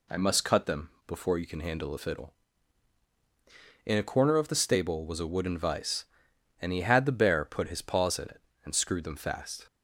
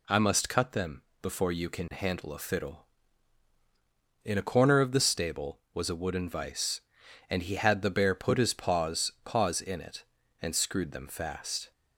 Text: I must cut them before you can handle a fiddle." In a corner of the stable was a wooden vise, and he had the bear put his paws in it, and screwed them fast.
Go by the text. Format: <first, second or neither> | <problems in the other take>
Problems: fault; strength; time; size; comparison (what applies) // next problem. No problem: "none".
first | pauses between "them" and "before"; slight; at 1.0 s; 0.22 s long; slight in the first // says "paws" twice; at 9.2 s